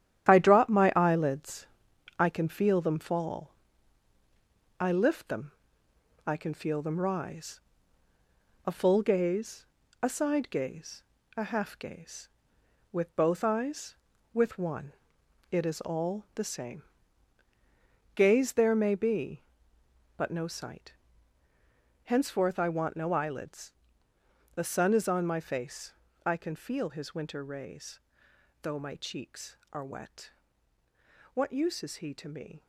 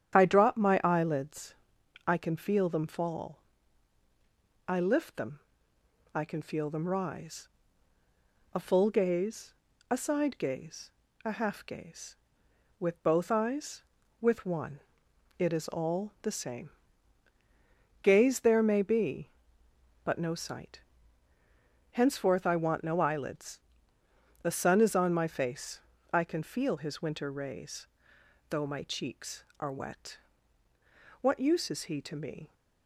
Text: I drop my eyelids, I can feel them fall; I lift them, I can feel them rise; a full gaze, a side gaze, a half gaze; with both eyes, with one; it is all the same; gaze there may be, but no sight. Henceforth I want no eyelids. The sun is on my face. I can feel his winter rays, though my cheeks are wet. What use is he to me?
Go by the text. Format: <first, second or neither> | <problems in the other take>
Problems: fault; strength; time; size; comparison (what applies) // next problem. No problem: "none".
second | gets quieter; strong; throughout; 8 dB // starts louder than the rest; strong; until 1.3 s; 11 dB; strong in the second